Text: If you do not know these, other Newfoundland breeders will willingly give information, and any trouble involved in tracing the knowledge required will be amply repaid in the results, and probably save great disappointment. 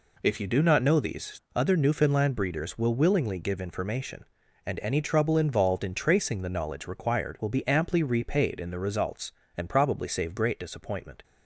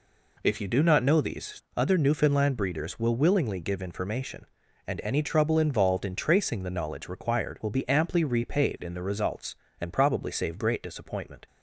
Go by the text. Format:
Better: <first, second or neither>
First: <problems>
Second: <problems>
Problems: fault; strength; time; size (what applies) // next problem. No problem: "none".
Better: neither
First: none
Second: none